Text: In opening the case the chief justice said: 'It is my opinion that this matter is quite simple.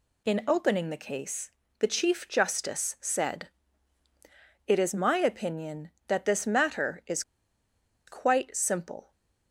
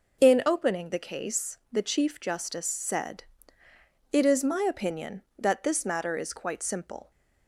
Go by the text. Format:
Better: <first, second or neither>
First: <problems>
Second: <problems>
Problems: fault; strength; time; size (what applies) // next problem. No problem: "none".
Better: second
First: pauses between "case" and "the"; slight; at 1.5 s; 0.28 s long // pauses between "is" and "quite"; noticeable; at 7.2 s; 0.84 s long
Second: none